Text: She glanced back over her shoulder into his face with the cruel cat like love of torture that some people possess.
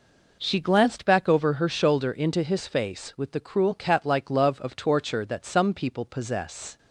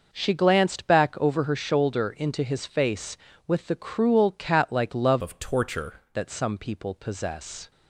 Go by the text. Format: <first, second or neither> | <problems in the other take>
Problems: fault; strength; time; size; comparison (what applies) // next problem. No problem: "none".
first | changes voice from "of" to "torture"; from 5.2 to 5.9 s; 0.7 s long